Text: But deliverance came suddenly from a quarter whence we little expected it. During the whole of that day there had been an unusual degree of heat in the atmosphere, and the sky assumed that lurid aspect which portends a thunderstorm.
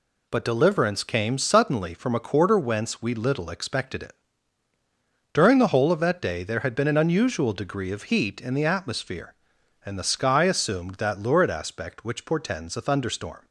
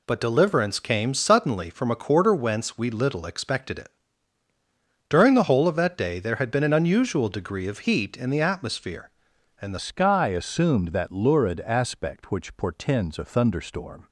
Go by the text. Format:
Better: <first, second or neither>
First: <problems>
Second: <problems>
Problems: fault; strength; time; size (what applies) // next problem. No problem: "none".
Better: first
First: none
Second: changes voice at "sky"; from 9.7 s on; 4.3 s long